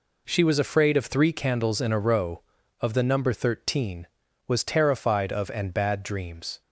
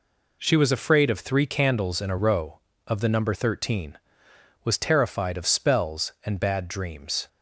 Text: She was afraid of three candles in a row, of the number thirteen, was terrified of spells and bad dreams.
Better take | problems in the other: second | skips "spells"; at 5.5 s

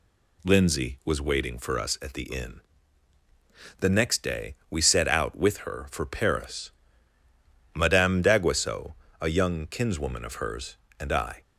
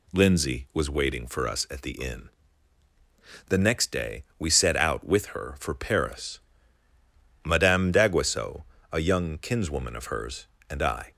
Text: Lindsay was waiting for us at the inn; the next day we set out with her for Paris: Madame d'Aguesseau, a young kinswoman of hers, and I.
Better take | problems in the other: neither | none

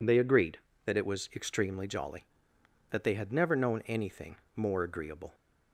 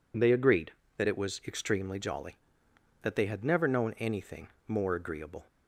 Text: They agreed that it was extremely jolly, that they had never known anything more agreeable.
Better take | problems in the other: neither | pauses between "anything" and "more"; slight; the same in both

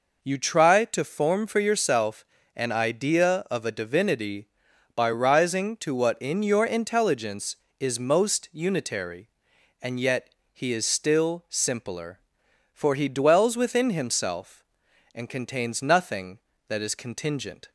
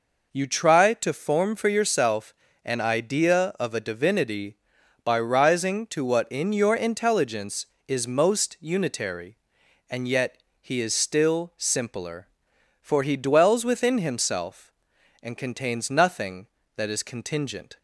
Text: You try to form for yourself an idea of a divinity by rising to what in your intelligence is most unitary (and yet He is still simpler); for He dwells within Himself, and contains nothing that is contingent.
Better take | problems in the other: neither | pauses between "yourself" and "an"; slight; the same in both // pauses between "yet" and "He"; slight; the same in both

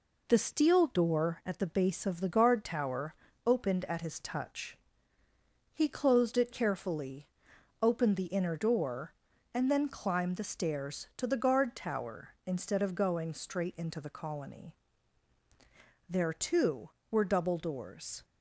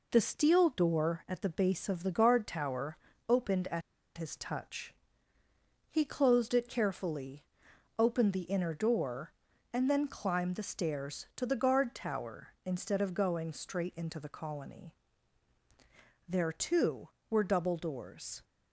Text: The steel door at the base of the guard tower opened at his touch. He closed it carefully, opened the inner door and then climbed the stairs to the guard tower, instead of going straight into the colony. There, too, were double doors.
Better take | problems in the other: first | pauses between "tower" and "opened"; slight; at 2.9 s; 0.30 s long; slight in the first // pauses between "at" and "his"; slight; at 3.8 s; 0.35 s long

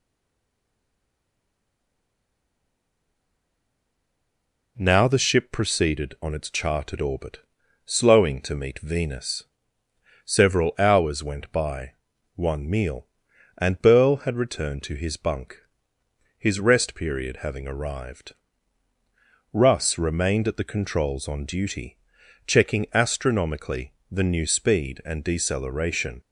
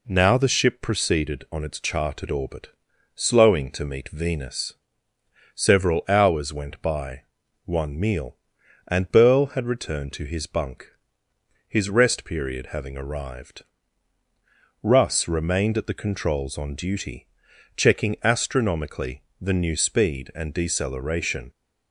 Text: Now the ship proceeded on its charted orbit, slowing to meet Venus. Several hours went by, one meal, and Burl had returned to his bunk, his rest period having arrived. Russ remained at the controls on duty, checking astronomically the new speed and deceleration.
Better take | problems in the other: second | stays silent before the first word; strong; until 4.7 s; 4.7 s long // pauses between "astronomically" and "the"; slight; at 23.9 s; 0.16 s long; slight in the second

